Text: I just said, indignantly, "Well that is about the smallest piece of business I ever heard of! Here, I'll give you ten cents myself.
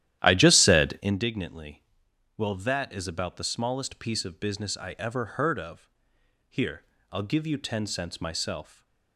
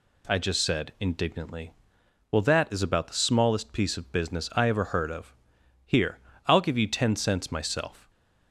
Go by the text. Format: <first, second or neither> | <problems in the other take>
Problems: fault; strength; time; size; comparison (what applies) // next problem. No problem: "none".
second | starts louder than the rest; strong; until 1.1 s; 12.5 dB // stays silent after the last word; slight; from 8.6 s on; 0.5 s long